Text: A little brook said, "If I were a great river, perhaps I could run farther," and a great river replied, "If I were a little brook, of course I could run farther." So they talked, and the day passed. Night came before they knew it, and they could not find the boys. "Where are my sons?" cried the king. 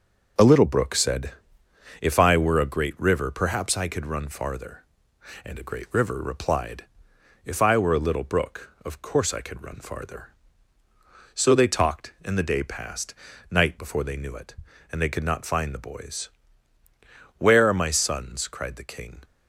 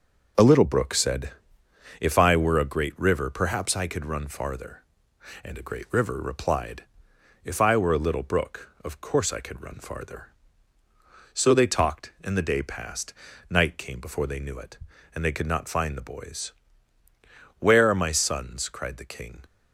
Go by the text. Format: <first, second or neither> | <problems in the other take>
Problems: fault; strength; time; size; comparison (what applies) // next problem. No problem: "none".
second | skips "came"; at 13.7 s